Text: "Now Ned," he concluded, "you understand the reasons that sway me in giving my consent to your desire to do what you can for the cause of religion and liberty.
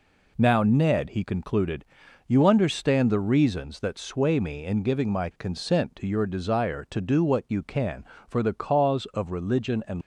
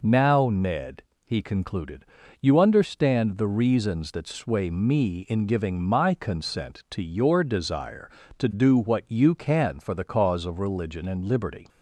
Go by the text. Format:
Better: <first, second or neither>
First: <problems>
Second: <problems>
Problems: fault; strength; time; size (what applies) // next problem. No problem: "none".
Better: second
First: stops before "liberty"; at 10.0 s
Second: none